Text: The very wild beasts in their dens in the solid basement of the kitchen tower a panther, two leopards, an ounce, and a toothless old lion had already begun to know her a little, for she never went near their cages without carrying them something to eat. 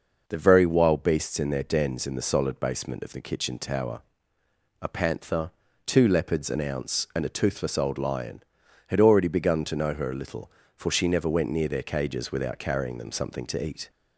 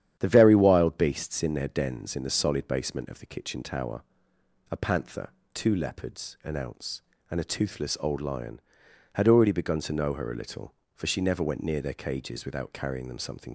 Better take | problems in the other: first | starts louder than the rest; strong; until 1.2 s; 10 dB // pauses between "tower" and "a"; noticeable; at 4.0 s; 0.70 s long; noticeable in the first // stops before "to eat"; at 13.4 s

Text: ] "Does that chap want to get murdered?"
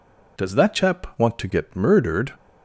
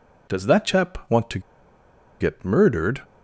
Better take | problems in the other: first | pauses between "to" and "get"; noticeable; at 1.3 s; 0.80 s long

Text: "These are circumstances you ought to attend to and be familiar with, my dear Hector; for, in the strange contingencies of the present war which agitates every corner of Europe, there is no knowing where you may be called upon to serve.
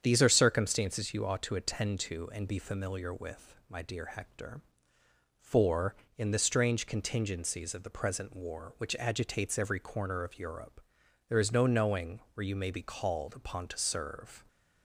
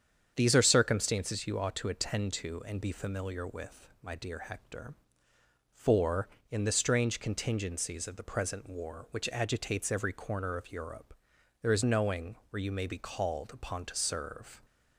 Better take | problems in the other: first | starts louder than the rest; strong; until 1.3 s; 8 dB; strong in the first // skips "no"; at 11.8 s

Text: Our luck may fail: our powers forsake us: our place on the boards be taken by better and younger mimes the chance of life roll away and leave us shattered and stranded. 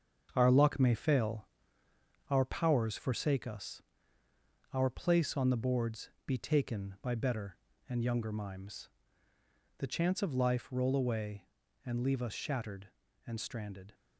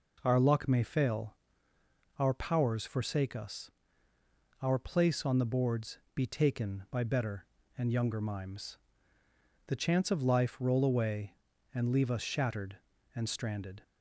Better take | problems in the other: second | gets quieter; throughout; 6.5 dB // pauses between "boards" and "be"; slight; at 6.0 s; 0.18 s long; slight in the second // pauses between "mimes" and "the"; noticeable; at 8.8 s; 0.88 s long; noticeable in the second

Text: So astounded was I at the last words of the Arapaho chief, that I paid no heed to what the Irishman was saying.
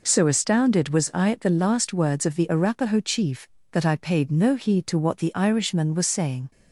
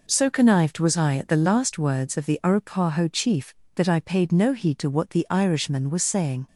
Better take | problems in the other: first | says "connived" for "astounded"; at 0.3 s

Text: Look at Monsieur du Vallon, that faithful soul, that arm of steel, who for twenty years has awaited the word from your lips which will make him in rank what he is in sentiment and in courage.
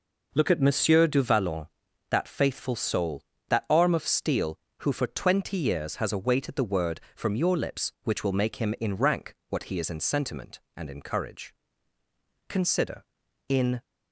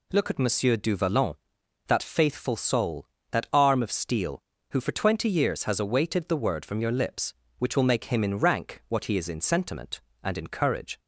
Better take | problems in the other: second | goes on to say "Consider in"; from 12.4 s on; 1.3 s long

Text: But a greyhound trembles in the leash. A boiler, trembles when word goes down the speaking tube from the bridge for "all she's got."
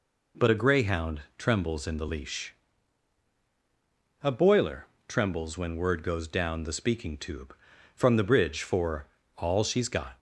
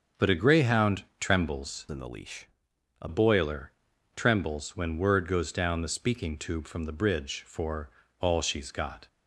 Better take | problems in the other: first | starts louder than the rest; until 1.3 s; 7 dB // pauses between "greyhound" and "trembles"; slight; at 1.0 s; 0.16 s long; slight in the first // changes voice from "in" to "A"; from 1.8 to 3.0 s; 1.2 s long // pauses between "for" and "all"; slight; at 7.8 s; 0.32 s long; slight in the first

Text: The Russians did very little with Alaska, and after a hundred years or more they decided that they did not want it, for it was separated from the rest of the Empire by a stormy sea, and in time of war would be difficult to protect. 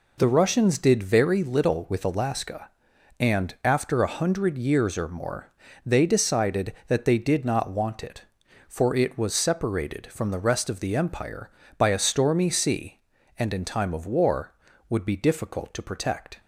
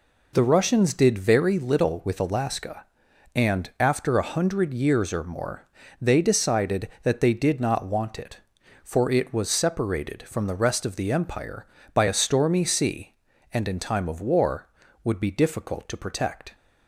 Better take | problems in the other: neither | pauses between "more" and "they"; slight; the same in both

